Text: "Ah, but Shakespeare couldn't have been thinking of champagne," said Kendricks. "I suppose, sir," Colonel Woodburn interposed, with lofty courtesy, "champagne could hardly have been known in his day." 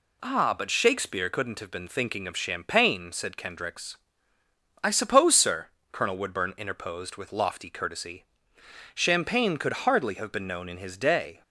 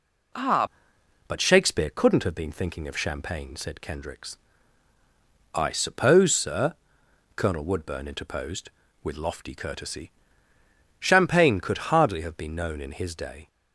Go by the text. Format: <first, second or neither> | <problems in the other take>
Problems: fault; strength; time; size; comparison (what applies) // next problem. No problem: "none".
first | changes voice at "but"; from 1.2 s on; 12.2 s long